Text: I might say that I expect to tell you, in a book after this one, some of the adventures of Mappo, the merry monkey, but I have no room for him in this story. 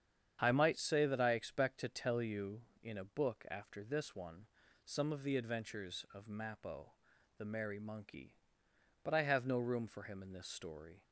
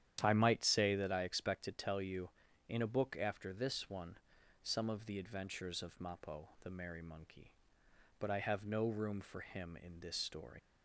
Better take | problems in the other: first | starts louder than the rest; strong; until 1.2 s; 10.5 dB; strong in the first // leaves "story" unfinished; at 10.5 s; 80 ms

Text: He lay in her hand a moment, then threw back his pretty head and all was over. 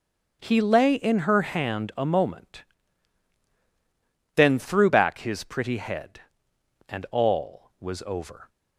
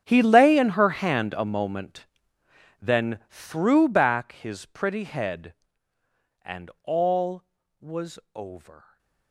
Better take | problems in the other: first | gets quieter; strong; throughout; 19 dB // starts louder than the rest; strong; until 1.0 s; 9 dB; strong in the first // pauses between "was" and "over"; slight; at 8.1 s; 0.16 s long // stays silent after the last word; slight; from 8.7 s on; 0.6 s long

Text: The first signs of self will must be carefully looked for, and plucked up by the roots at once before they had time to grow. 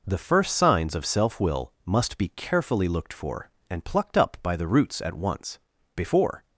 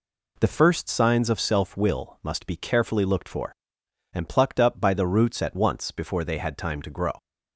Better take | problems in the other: second | pauses between "once" and "before"; at 5.5 s; 0.38 s long // stops before "they had time to grow"; at 6.4 s

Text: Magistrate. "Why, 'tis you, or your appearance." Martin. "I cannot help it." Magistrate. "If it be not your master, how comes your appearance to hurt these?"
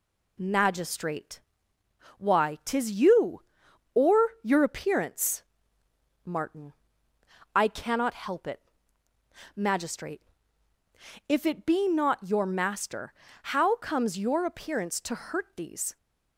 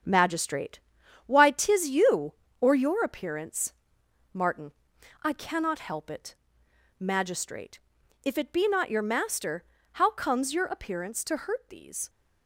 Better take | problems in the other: first | gets quieter; throughout; 7 dB

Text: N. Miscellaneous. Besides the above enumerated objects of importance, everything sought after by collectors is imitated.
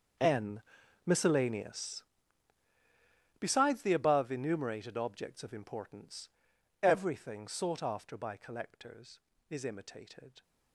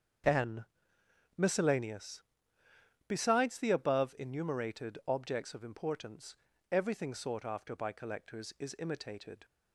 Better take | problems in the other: second | gets quieter; strong; throughout; 17.5 dB // starts louder than the rest; until 1.6 s; 6.5 dB; strong in the second

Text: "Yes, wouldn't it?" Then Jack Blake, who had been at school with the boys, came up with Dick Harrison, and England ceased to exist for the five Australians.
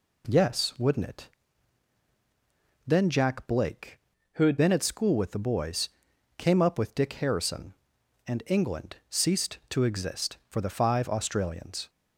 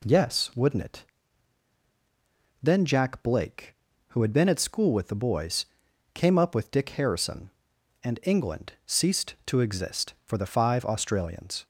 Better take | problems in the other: second | changes voice from "who" to "had"; from 4.3 to 4.5 s; 0.2 s long

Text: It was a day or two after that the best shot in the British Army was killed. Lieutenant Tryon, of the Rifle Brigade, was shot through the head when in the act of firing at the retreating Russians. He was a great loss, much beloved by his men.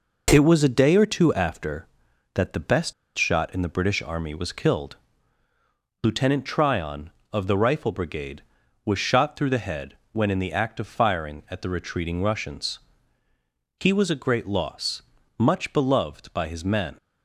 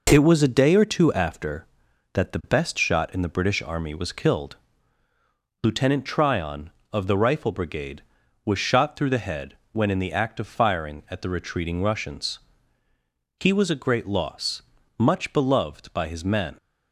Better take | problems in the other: second | pauses between "best" and "shot"; slight; at 2.9 s; 0.23 s long // pauses between "head" and "when"; slight; at 9.9 s; 0.16 s long; slight in the second

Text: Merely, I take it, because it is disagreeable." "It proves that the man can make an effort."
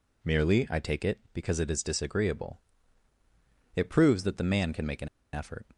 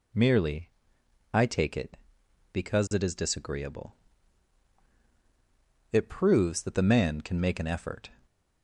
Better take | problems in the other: second | pauses between "an" and "effort"; slight; at 5.0 s; 0.25 s long

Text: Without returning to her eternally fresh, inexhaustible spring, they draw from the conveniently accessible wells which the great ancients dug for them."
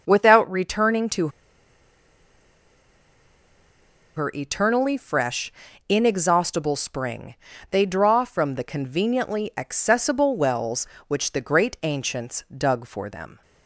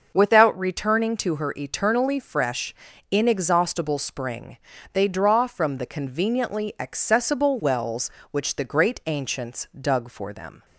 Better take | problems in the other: second | starts louder than the rest; until 1.0 s; 6.5 dB; also in the second // pauses between "to" and "her"; strong; at 1.2 s; 2.8 s long

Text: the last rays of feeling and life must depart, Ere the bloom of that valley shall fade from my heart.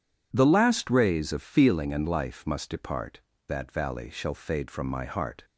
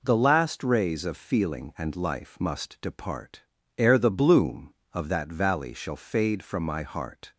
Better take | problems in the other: second | skips "Ere the bloom of"; at 3.3 s

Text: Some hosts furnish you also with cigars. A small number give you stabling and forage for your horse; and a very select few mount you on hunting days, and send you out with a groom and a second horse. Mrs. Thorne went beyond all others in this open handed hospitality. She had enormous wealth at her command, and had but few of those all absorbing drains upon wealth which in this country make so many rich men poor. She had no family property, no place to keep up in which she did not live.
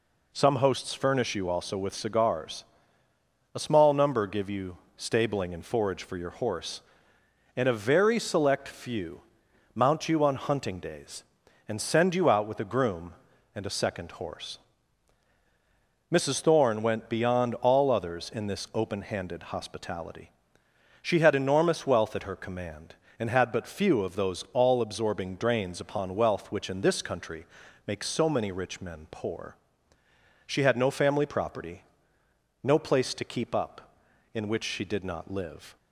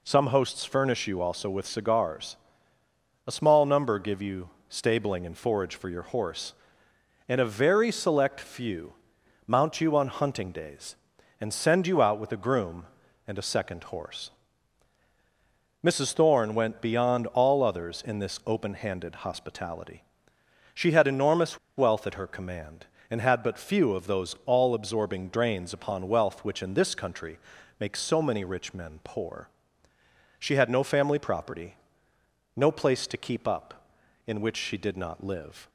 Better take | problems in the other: first | pauses between "you" and "stabling"; slight; at 4.4 s; 0.18 s long; slight in the first // pauses between "few" and "mount"; noticeable; at 8.9 s; 0.54 s long; noticeable in the first // pauses between "enormous" and "wealth"; slight; at 21.5 s; 0.19 s long // pauses between "country" and "make"; at 27.3 s; 0.42 s long; also in the first

